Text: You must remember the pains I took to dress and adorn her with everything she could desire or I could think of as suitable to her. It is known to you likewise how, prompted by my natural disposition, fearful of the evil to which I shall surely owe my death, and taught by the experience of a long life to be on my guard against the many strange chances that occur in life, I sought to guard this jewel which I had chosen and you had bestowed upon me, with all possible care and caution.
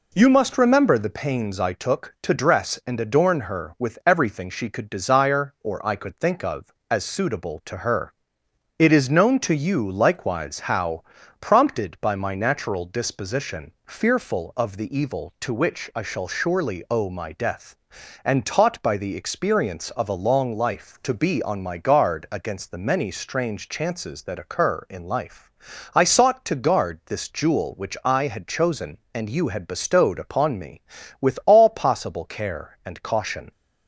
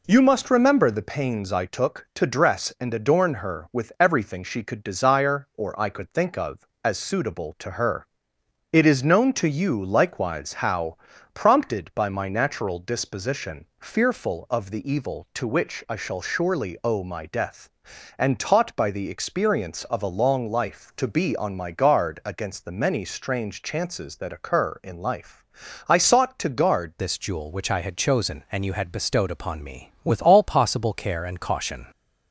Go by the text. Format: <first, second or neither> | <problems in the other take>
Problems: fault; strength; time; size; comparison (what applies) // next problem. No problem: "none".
first | changes voice at "this"; from 26.9 s on; 4.9 s long